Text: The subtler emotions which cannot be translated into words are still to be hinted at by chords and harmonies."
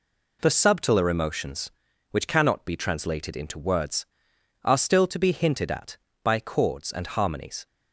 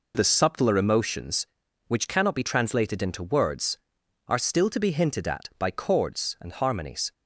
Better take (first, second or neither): neither